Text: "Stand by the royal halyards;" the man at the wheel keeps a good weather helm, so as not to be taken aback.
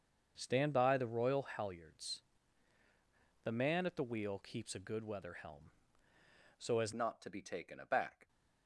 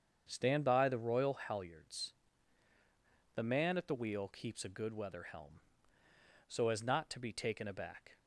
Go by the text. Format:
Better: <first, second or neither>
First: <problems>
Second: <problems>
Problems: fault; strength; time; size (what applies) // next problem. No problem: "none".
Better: second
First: starts louder than the rest; until 1.3 s; 6.5 dB // changes voice at "not"; from 6.9 s on; 1.3 s long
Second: starts louder than the rest; strong; until 1.3 s; 7 dB